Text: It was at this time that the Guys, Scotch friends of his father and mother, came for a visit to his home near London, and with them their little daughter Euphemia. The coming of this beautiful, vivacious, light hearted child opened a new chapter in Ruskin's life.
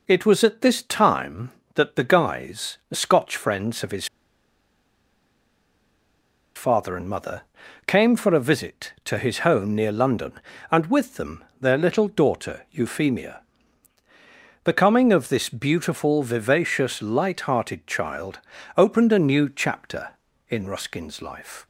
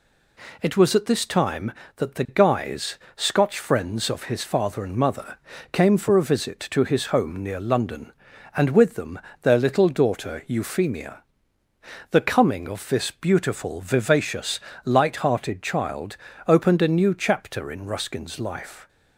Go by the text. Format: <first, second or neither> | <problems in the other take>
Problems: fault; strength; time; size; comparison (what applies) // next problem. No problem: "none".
second | pauses between "his" and "father"; strong; at 4.0 s; 2.5 s long // pauses between "them" and "their"; slight; at 11.4 s; 0.18 s long; slight in the second // pauses between "child" and "opened"; at 18.3 s; 0.38 s long; slight in the second